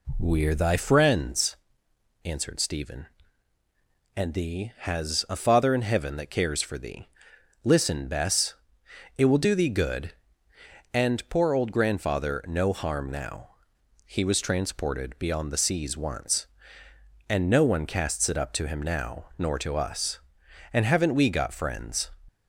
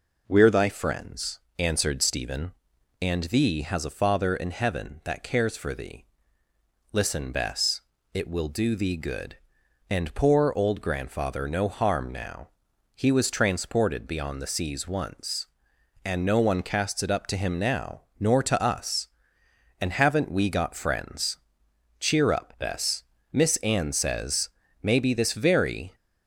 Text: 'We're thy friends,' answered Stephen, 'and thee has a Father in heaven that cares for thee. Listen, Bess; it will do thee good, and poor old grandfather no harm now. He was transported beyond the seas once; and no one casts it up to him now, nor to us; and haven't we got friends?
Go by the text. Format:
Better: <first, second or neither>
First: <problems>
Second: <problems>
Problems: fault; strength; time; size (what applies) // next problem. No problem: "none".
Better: first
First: none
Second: goes on to say "Cheer up Bess Miss Anne says maybe this very"; strong; from 21.9 s on; 3.9 s long